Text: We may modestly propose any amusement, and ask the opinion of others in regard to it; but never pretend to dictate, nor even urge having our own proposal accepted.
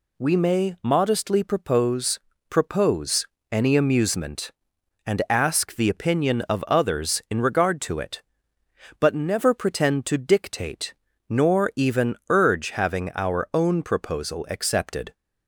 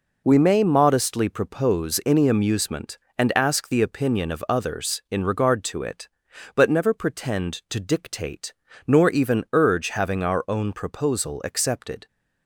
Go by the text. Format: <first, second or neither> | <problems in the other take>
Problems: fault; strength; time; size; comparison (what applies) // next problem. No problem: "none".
second | says "propose" twice; at 2.4 s